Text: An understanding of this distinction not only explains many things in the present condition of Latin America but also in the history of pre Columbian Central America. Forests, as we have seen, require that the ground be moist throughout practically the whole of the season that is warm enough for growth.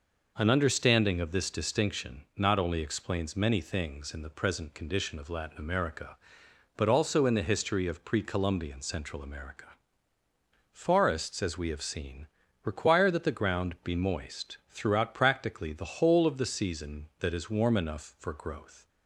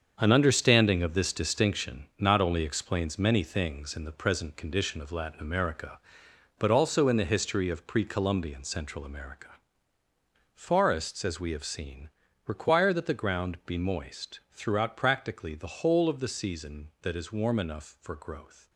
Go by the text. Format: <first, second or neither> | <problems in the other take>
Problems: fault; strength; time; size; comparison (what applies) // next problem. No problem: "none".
first | gets quieter; strong; throughout; 9.5 dB